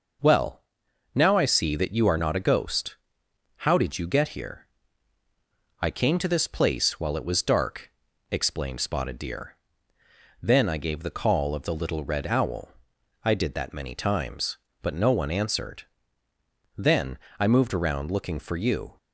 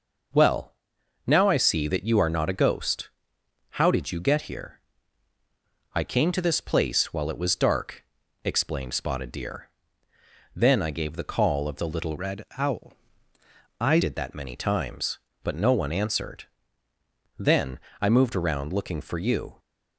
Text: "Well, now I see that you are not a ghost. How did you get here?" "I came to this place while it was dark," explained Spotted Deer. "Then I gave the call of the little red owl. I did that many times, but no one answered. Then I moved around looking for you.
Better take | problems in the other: first | changes voice from "red" to "I"; from 12.1 to 13.9 s; 1.8 s long // pauses between "Then" and "I"; slight; at 17.7 s; 0.20 s long; slight in the first

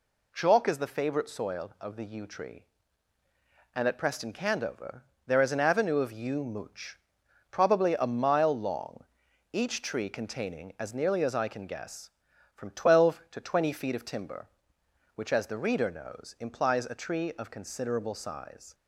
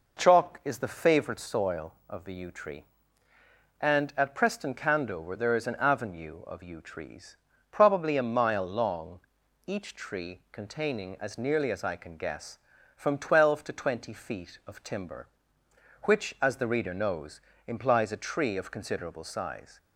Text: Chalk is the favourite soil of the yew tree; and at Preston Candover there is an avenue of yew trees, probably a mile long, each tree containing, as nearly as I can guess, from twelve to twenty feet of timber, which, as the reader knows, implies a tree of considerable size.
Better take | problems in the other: second | pauses between "Candover" and "there"; slight; at 5.0 s; 0.22 s long // says "mooch" for "trees"; at 6.4 s

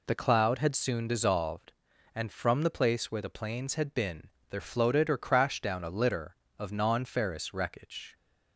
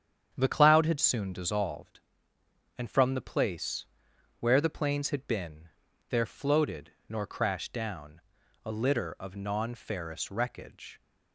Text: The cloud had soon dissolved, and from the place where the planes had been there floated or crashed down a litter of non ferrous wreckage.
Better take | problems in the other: first | starts louder than the rest; strong; until 1.3 s; 8.5 dB // pauses between "place" and "where"; noticeable; at 3.8 s; 0.56 s long // pauses between "been" and "there"; at 5.6 s; 0.40 s long; slight in the first // says "nor" for "or"; at 7.0 s // pauses between "down" and "a"; at 8.2 s; 0.42 s long

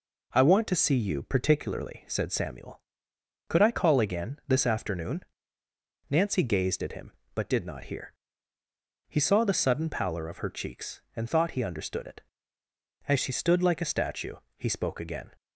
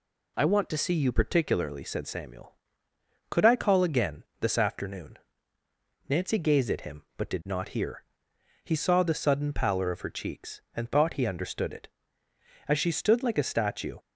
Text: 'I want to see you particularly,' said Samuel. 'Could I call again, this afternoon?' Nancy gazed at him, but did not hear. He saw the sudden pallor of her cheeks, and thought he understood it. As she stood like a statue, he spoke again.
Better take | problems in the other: first | stops before "he spoke again"; at 13.9 s

